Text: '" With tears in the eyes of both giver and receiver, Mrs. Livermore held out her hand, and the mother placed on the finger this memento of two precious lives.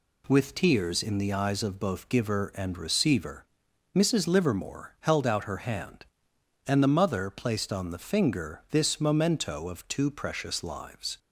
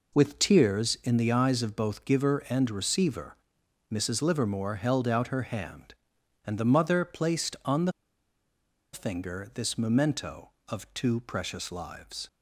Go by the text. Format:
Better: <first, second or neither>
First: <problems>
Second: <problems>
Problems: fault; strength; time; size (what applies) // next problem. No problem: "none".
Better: first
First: none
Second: pauses between "the" and "finger"; at 7.9 s; 1.0 s long